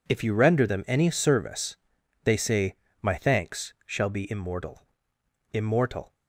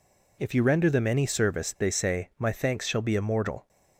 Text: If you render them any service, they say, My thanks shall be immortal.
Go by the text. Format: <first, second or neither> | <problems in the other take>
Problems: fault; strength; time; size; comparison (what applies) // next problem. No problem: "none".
second | says "immortal" twice; at 5.5 s